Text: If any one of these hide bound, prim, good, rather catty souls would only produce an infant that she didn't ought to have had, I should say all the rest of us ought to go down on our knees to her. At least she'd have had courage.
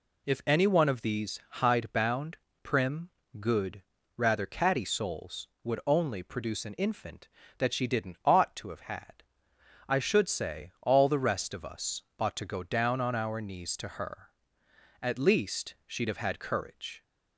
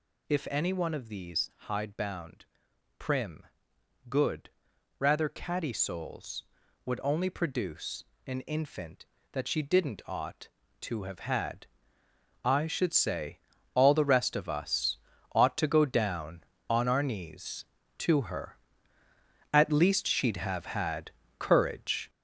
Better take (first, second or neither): first